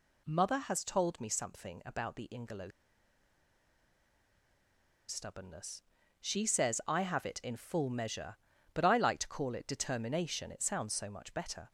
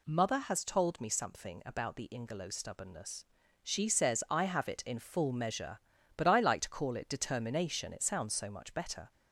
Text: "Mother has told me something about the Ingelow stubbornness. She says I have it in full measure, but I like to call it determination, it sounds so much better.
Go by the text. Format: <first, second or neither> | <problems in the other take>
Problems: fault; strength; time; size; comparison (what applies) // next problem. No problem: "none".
second | pauses between "Ingelow" and "stubbornness"; strong; at 2.6 s; 2.3 s long